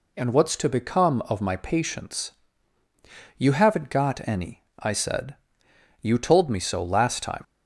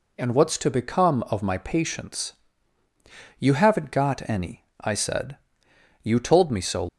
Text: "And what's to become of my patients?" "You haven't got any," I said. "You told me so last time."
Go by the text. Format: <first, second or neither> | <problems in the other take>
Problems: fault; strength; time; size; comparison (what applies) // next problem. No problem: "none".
first | stops before "last time"; at 6.8 s